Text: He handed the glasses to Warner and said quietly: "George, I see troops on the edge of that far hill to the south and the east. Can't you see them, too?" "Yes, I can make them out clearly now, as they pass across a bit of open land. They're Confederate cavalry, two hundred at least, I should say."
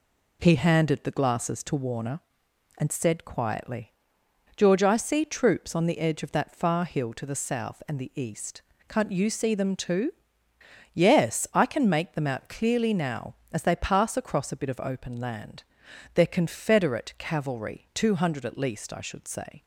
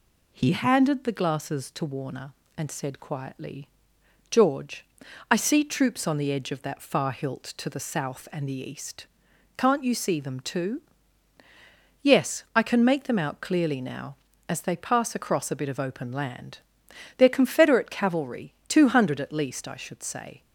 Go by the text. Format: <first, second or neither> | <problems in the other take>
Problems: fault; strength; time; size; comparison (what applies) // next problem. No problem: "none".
first | says "hilt" for "hill"; at 7.1 s